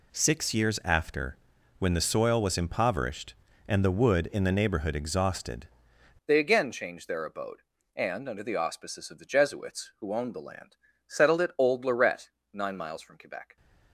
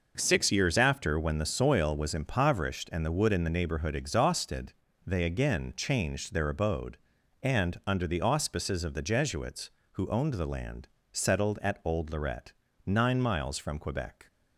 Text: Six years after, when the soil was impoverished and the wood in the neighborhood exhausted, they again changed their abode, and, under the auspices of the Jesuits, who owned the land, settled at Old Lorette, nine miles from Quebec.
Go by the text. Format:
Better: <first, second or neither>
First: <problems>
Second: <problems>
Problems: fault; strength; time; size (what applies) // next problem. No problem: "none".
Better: second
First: changes voice at "they"; from 6.2 s on; 7.3 s long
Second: none